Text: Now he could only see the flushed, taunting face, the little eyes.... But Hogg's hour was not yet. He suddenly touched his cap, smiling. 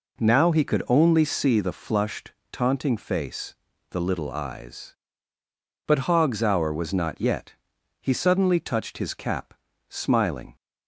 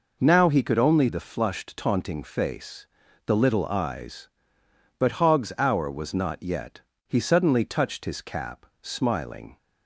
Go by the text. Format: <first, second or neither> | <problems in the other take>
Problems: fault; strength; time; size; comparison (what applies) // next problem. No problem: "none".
first | skips "see"; at 1.0 s